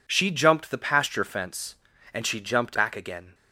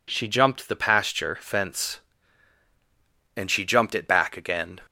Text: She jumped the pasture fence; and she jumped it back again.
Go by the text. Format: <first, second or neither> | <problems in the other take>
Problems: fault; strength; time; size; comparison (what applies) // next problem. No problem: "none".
second | skips "it"; at 2.7 s